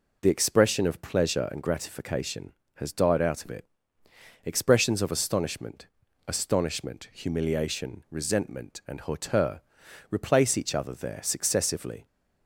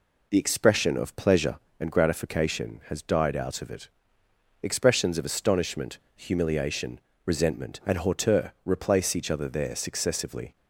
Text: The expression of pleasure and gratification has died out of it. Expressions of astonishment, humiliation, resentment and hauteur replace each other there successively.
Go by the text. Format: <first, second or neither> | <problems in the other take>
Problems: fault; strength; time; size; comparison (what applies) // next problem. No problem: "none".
second | says "astonishment" twice; at 6.2 s // pauses between "hauteur" and "replace"; noticeable; at 9.6 s; 0.48 s long